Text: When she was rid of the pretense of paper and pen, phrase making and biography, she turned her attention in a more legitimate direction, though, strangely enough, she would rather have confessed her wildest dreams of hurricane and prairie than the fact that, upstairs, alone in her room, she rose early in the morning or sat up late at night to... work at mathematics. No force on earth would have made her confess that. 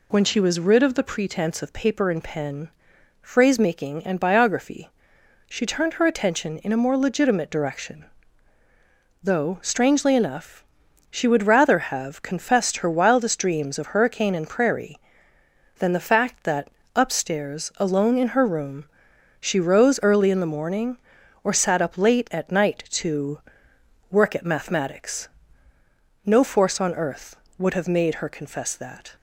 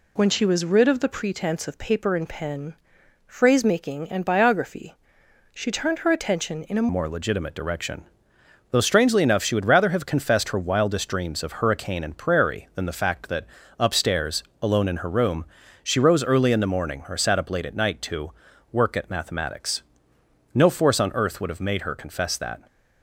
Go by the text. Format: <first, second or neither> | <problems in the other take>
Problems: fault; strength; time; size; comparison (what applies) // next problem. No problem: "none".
first | changes voice at "more"; from 6.8 s on; 15.8 s long